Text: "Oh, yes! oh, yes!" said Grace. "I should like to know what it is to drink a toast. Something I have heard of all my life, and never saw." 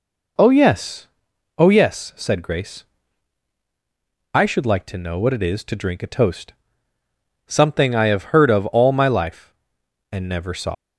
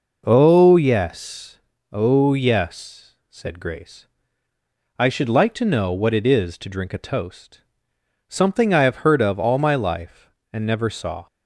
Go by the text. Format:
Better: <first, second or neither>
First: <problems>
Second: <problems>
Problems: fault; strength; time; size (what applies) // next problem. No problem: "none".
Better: second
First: leaves "saw" unfinished; at 10.7 s; 120 ms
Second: none